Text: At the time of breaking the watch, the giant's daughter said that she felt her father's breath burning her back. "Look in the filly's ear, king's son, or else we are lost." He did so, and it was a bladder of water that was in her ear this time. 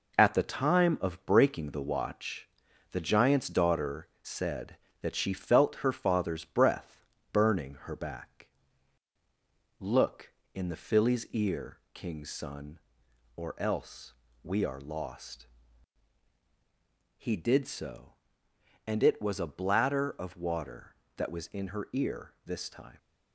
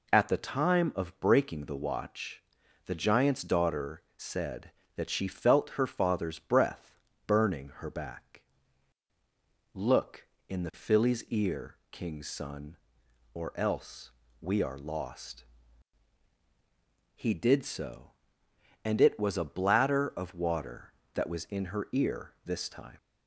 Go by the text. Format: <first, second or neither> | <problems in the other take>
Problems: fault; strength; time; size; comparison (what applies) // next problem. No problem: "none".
second | gets quieter; noticeable; throughout; 6 dB // pauses between "breath" and "burning"; slight; at 7.0 s; 0.28 s long; slight in the second // pauses between "else" and "we"; slight; at 14.1 s; 0.30 s long; slight in the second